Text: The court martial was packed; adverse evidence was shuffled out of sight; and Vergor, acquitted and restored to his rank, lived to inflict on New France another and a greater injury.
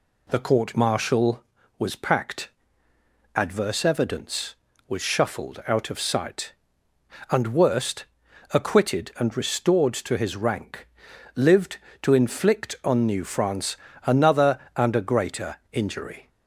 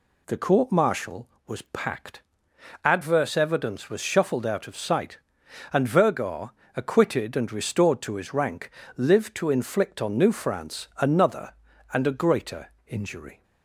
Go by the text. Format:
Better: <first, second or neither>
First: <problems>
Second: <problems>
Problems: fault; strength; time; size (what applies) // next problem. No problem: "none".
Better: second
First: says "Worst" for "Vergor"; at 7.5 s // pauses between "France" and "another"; slight; at 13.7 s; 0.26 s long // pauses between "greater" and "injury"; slight; at 15.5 s; 0.16 s long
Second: pauses between "greater" and "injury"; slight; at 12.7 s; 0.16 s long